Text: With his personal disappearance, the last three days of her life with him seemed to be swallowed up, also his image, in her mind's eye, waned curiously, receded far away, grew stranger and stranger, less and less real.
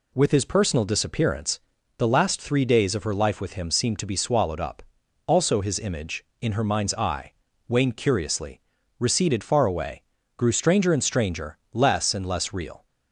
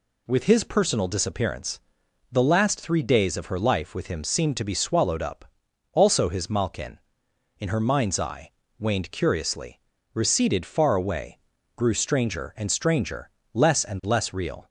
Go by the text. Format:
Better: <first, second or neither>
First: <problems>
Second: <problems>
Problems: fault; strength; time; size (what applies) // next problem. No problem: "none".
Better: first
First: none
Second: says "malkin" for "image"; at 6.4 s